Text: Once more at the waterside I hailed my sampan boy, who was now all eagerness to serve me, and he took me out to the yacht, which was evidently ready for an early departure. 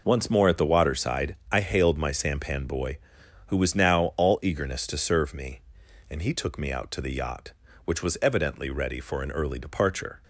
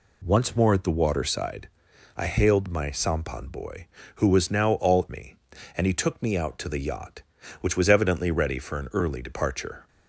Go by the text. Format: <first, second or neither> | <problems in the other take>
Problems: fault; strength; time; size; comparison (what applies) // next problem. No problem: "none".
first | pauses between "waterside" and "I"; noticeable; at 1.6 s; 0.50 s long; slight in the first // skips "eagerness to serve"; at 5.0 s